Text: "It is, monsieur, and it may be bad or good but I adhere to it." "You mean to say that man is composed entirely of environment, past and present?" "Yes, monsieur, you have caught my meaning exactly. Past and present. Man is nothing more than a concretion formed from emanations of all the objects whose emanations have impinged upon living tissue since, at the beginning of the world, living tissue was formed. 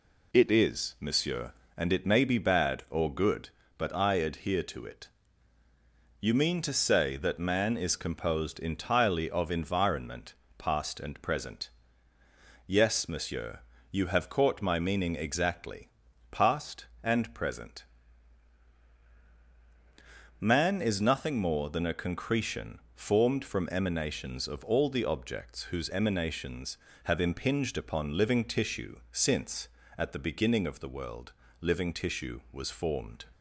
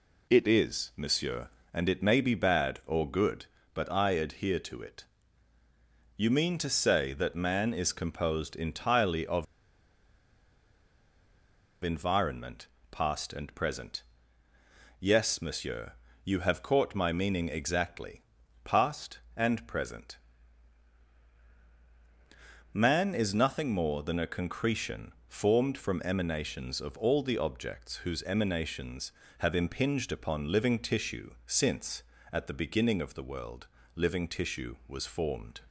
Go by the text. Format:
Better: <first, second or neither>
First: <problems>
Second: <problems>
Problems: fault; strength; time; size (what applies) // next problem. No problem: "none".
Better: first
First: pauses between "concretion" and "formed"; slight; at 22.7 s; 0.16 s long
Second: pauses between "of" and "environment"; strong; at 9.4 s; 2.3 s long // pauses between "concretion" and "formed"; slight; at 25.1 s; 0.16 s long